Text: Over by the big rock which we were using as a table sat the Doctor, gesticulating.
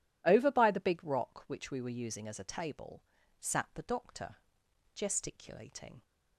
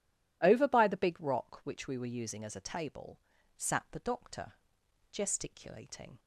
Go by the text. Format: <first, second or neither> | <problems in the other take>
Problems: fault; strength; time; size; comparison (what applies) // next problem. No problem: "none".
neither | pauses between "table" and "sat"; the same in both